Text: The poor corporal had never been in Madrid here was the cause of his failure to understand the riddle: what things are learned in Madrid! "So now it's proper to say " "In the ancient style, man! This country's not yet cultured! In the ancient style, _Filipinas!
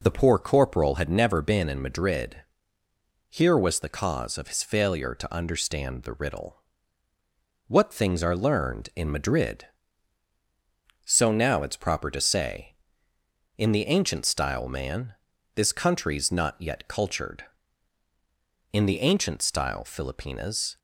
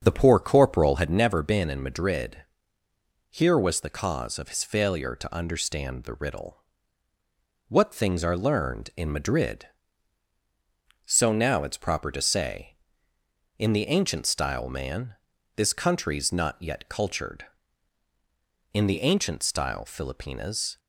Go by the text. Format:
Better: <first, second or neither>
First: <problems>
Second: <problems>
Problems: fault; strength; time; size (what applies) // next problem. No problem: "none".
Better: first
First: pauses between "Madrid" and "here"; noticeable; at 2.3 s; 0.92 s long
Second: starts louder than the rest; until 1.3 s; 7 dB // pauses between "Madrid" and "here"; noticeable; at 2.3 s; 0.92 s long